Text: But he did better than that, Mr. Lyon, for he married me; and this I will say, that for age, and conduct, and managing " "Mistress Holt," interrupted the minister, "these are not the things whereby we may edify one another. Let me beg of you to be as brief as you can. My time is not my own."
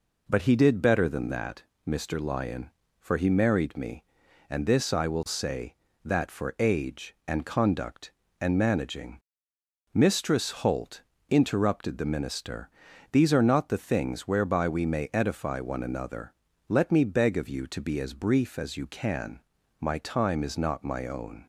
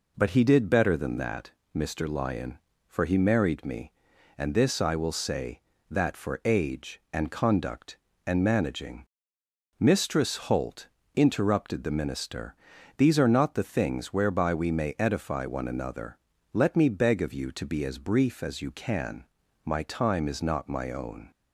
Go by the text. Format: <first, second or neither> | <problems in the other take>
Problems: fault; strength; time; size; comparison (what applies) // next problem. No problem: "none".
neither | none